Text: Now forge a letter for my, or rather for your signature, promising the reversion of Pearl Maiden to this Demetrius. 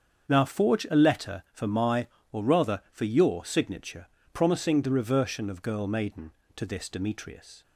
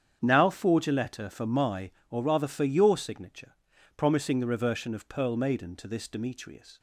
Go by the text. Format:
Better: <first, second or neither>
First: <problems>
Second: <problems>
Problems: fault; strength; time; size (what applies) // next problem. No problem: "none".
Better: second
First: starts louder than the rest; strong; until 1.3 s; 7 dB // says "Girl" for "Pearl"; at 5.6 s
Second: starts louder than the rest; strong; until 1.2 s; 8.5 dB